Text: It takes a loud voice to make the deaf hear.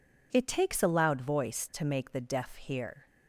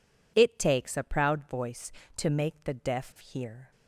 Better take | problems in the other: first | says "proud" for "loud"; at 1.0 s

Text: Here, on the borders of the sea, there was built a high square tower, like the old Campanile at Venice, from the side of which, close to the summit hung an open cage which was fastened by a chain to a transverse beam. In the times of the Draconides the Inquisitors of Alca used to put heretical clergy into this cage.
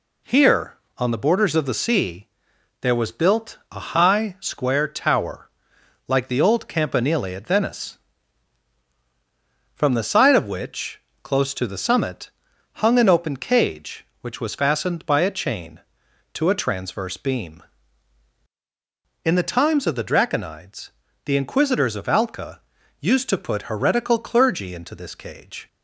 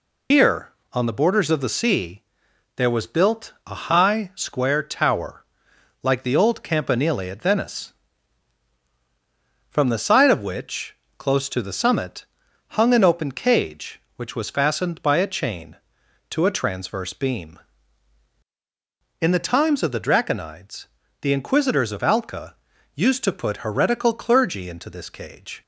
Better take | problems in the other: first | loses the start of "Here"; at 0.3 s; 110 ms // pauses between "summit" and "hung"; noticeable; at 12.2 s; 0.48 s long; noticeable in the first // pauses between "Draconides" and "the"; slight; at 20.8 s; 0.34 s long; slight in the first // pauses between "Alca" and "used"; at 22.5 s; 0.40 s long; also in the first

